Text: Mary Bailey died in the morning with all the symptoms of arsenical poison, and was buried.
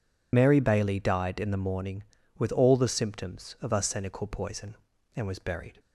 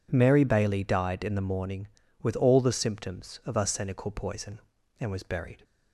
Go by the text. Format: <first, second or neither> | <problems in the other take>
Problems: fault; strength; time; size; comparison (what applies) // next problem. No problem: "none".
second | loses the start of "Mary"; at 0.3 s; 90 ms